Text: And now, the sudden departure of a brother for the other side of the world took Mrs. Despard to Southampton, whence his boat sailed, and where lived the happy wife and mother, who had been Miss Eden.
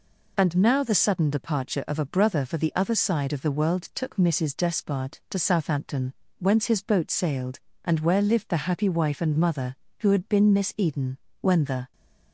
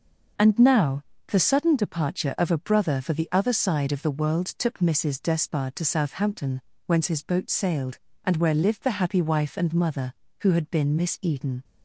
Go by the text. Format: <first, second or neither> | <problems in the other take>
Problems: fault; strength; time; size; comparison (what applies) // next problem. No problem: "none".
second | goes on to say "When the"; from 11.4 s on; 0.50 s long